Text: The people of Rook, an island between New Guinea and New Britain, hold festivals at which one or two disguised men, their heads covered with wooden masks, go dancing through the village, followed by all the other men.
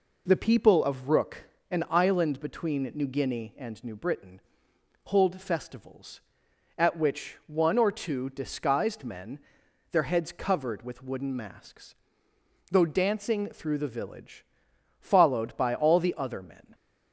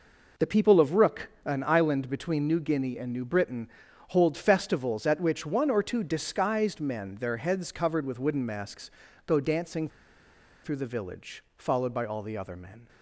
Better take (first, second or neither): first